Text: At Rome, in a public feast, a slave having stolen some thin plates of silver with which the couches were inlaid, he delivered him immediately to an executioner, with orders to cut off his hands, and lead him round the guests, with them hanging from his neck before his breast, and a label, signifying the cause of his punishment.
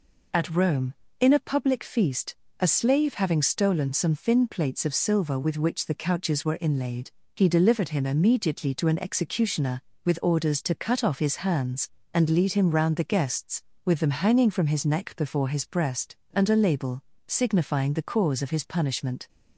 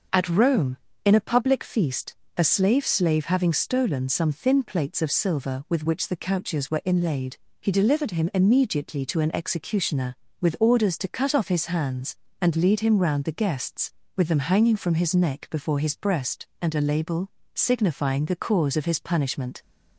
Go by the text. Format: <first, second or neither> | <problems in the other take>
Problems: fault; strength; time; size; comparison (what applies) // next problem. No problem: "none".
first | starts louder than the rest; until 1.3 s; 6 dB // says "slave" twice; at 2.8 s